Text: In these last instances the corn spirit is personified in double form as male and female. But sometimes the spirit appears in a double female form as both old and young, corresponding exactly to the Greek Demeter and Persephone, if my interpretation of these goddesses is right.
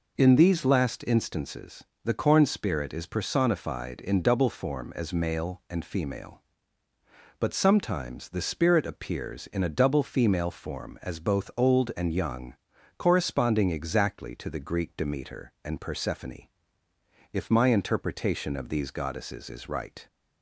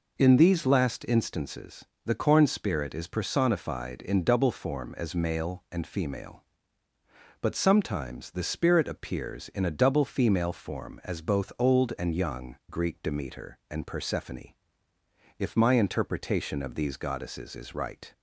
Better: first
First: pauses between "instances" and "the"; slight; at 1.8 s; 0.22 s long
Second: pauses between "instances" and "the"; slight; at 1.8 s; 0.22 s long // skips "corresponding exactly to the"; at 12.6 s

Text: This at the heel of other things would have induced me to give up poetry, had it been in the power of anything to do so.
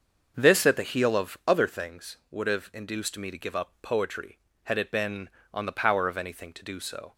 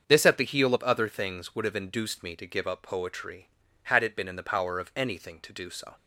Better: second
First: starts louder than the rest; until 1.3 s; 6.5 dB // says "on" for "in"; at 5.5 s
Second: starts louder than the rest; until 1.0 s; 7 dB

